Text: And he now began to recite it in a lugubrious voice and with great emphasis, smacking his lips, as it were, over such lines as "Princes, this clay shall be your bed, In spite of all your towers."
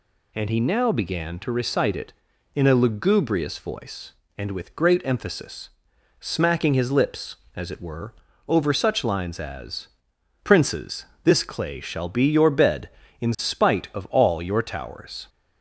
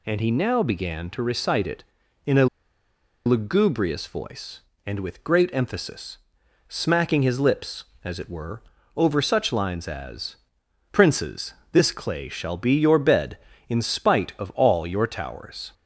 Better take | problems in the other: first | pauses between "a" and "lugubrious"; noticeable; at 2.4 s; 0.79 s long // pauses between "as" and "Princes"; noticeable; at 10.3 s; 0.54 s long; noticeable in the first

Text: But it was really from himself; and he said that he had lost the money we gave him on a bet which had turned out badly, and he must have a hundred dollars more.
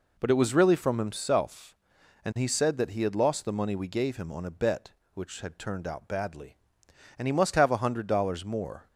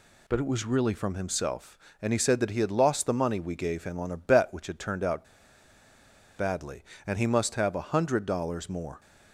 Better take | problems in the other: first | pauses between "out" and "badly"; at 5.2 s; 1.1 s long

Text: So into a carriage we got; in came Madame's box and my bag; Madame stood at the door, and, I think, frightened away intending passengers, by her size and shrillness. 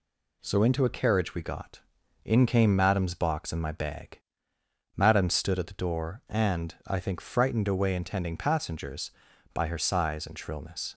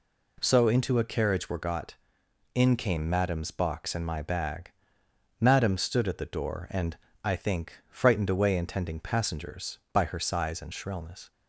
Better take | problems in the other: first | says "were" for "we"; at 1.4 s

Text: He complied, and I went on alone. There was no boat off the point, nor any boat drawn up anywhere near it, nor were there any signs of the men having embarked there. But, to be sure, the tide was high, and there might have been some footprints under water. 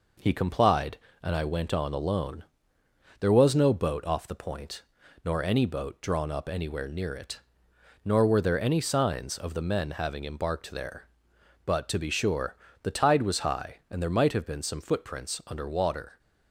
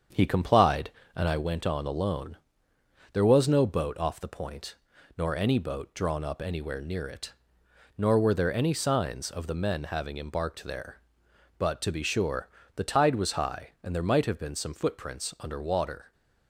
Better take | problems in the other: first | starts louder than the rest; strong; until 1.4 s; 7.5 dB

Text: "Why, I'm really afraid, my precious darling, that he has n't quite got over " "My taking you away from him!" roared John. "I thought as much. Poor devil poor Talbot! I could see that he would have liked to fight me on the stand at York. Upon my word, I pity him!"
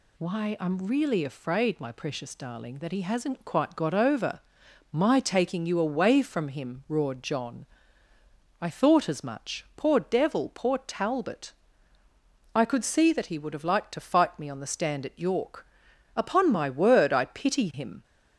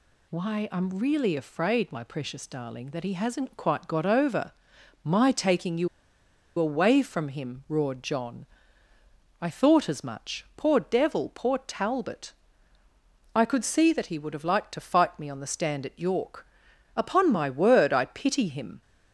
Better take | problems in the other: first | pauses between "you" and "away"; noticeable; at 5.8 s; 0.70 s long

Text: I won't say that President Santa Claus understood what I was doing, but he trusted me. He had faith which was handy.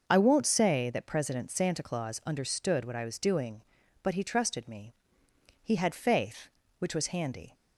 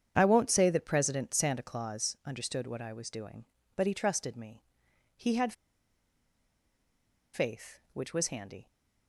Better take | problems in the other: first | starts louder than the rest; strong; until 1.1 s; 8 dB; noticeable in the first // pauses between "had" and "faith"; strong; at 5.5 s; 1.8 s long

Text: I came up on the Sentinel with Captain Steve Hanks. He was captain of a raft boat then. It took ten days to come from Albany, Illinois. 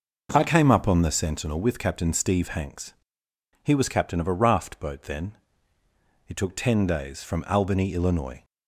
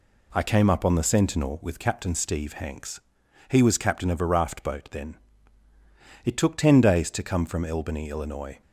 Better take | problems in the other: second | skips "to come"; at 7.2 s

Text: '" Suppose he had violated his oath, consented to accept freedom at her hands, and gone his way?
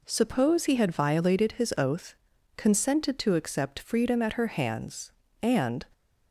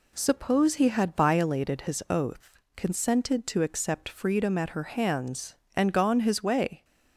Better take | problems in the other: second | stops before "gone his way"; at 5.9 s

